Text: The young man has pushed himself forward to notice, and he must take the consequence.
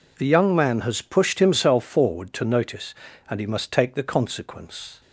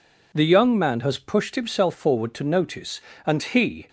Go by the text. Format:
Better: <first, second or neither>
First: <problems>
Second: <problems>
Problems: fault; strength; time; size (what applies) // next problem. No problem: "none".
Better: first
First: none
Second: stops before "must take the consequence"; at 3.8 s